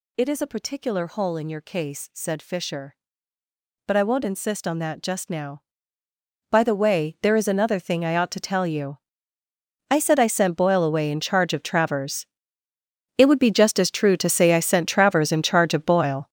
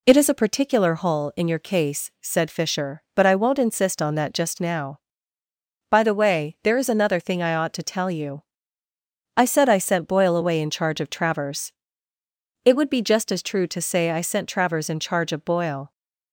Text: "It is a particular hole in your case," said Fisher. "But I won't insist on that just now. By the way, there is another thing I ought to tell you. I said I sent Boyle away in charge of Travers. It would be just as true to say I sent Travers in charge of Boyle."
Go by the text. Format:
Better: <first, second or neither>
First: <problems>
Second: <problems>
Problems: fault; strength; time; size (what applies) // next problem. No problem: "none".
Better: second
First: gets louder; strong; throughout; 11 dB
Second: none